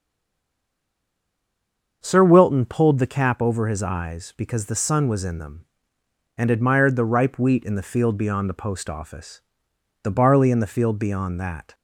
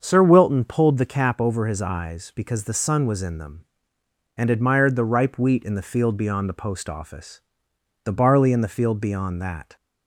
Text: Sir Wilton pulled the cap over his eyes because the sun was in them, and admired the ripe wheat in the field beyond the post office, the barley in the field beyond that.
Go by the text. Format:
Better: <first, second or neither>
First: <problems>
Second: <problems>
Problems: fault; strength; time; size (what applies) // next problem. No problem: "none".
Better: second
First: stays silent before the first word; noticeable; until 2.0 s; 2.0 s long // starts louder than the rest; until 3.0 s; 6.5 dB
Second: starts louder than the rest; until 1.0 s; 6.5 dB